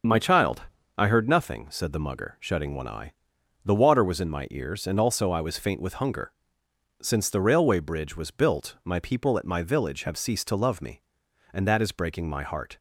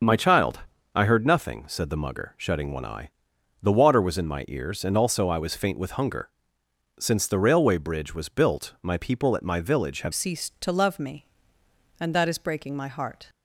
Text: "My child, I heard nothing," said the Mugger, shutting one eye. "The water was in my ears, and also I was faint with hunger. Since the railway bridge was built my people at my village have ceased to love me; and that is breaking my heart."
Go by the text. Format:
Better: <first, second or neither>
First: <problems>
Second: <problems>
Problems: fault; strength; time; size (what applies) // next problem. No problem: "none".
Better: first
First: starts louder than the rest; until 1.4 s; 6.5 dB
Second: starts louder than the rest; until 1.3 s; 6.5 dB // changes voice at "ceased"; from 10.1 s on; 3.1 s long